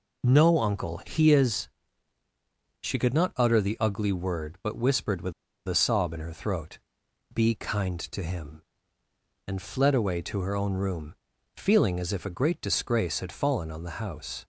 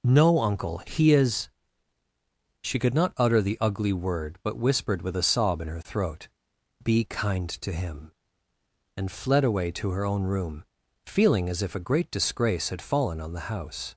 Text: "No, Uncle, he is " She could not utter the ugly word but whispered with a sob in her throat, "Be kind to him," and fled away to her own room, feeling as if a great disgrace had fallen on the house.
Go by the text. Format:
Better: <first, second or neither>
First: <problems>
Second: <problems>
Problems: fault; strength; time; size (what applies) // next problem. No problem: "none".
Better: second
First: pauses between "with" and "a"; slight; at 5.3 s; 0.33 s long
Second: none